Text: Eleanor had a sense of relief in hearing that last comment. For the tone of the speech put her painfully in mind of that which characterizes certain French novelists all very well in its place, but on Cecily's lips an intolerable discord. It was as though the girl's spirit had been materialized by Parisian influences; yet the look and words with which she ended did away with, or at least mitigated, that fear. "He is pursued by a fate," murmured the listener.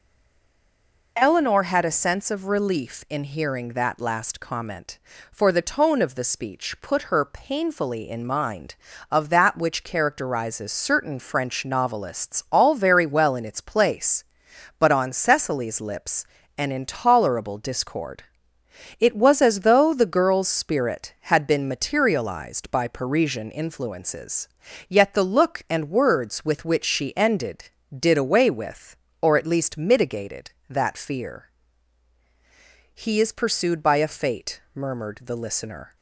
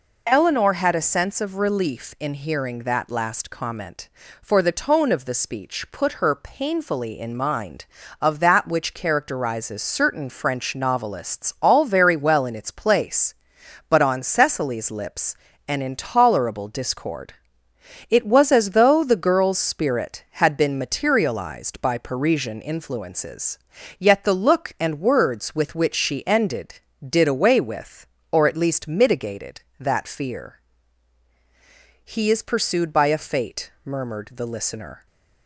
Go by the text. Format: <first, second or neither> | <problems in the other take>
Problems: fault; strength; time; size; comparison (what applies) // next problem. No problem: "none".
second | stays silent before the first word; until 1.1 s; 1.1 s long // pauses between "lips" and "an"; slight; at 16.2 s; 0.32 s long; slight in the second